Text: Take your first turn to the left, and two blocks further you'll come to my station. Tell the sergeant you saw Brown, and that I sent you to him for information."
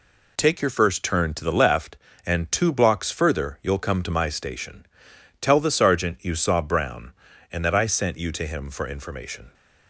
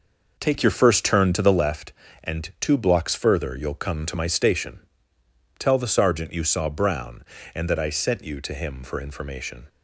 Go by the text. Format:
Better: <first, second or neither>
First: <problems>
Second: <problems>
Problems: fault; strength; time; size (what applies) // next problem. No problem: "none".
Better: first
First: none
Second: starts louder than the rest; noticeable; until 1.7 s; 5.5 dB